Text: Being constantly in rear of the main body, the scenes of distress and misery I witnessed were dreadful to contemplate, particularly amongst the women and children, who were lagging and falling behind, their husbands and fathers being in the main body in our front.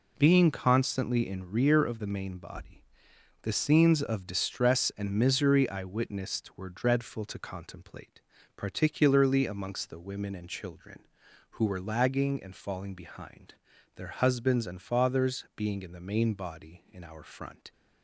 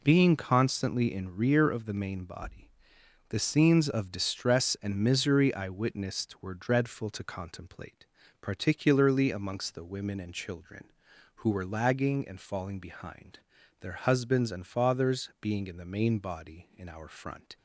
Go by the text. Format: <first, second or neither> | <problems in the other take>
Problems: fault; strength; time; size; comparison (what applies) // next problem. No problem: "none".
neither | none